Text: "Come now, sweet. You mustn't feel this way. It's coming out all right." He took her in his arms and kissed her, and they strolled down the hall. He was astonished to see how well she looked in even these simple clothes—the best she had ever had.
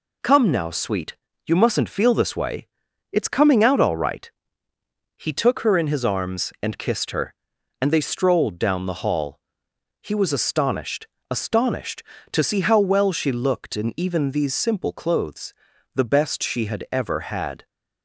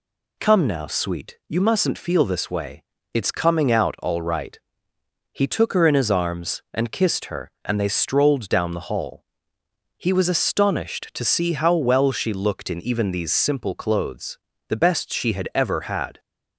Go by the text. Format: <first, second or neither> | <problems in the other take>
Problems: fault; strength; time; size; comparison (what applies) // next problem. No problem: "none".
second | says "astonished" twice; at 11.3 s